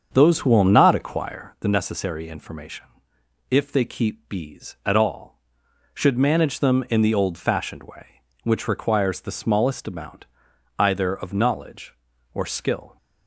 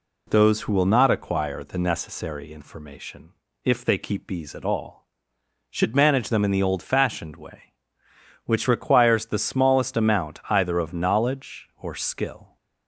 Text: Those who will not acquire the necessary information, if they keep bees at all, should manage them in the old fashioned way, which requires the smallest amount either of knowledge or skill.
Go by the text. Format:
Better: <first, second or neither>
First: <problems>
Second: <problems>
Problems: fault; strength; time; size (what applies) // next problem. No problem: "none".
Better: second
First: starts louder than the rest; until 1.6 s; 7 dB // pauses between "amount" and "either"; noticeable; at 10.2 s; 0.52 s long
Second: none